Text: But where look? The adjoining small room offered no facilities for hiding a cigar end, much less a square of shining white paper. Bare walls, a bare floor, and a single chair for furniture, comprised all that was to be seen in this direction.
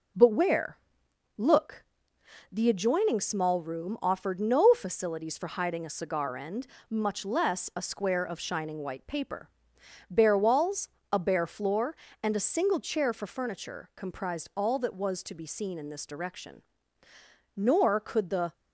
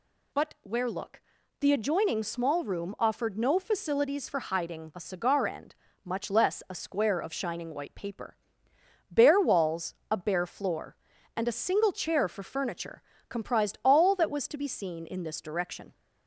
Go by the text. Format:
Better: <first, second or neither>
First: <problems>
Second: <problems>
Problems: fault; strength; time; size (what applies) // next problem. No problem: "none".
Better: second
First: pauses between "where" and "look"; noticeable; at 0.7 s; 0.60 s long // goes on to say "Nor could the"; noticeable; from 17.5 s on; 0.96 s long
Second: none